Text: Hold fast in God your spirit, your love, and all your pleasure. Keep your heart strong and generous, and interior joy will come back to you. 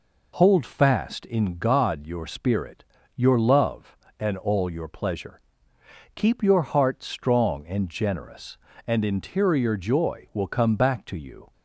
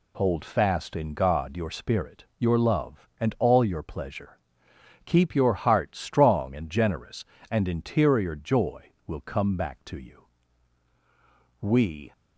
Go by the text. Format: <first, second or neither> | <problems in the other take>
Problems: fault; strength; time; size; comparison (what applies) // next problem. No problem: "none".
first | goes on to say "We"; from 11.5 s on; 0.52 s long